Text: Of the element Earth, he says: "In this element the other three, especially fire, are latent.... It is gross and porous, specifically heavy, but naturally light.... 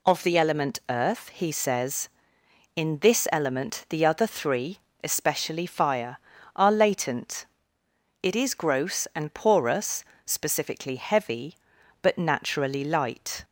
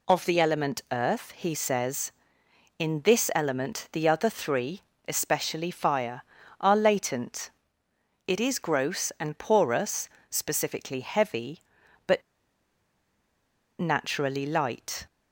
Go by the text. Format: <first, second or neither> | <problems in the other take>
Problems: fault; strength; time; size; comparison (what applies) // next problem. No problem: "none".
first | pauses between "but" and "naturally"; strong; at 12.2 s; 1.5 s long